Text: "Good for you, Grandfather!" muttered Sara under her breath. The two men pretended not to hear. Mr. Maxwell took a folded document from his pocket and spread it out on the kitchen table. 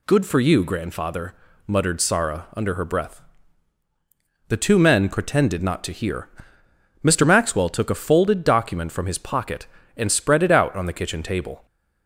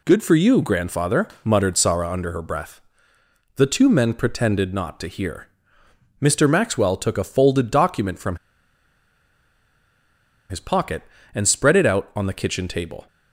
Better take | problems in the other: first | pauses between "from" and "his"; strong; at 8.3 s; 2.1 s long

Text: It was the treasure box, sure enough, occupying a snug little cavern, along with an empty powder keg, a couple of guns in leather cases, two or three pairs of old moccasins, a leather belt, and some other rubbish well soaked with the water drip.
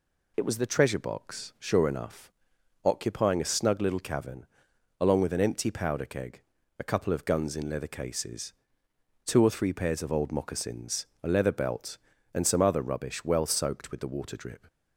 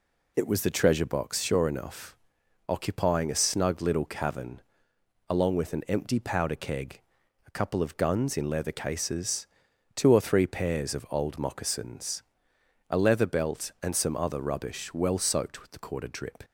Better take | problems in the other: first | says "quarter" for "water"; at 15.7 s

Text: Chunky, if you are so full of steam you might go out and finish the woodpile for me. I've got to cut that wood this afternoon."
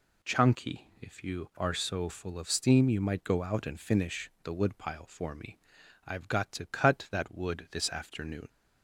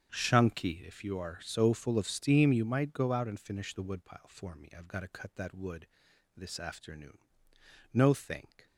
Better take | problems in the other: first | starts louder than the rest; strong; until 1.1 s; 8 dB // pauses between "wood" and "this"; noticeable; at 5.8 s; 0.50 s long // goes on to say "No thank"; noticeable; from 7.9 s on; 0.74 s long

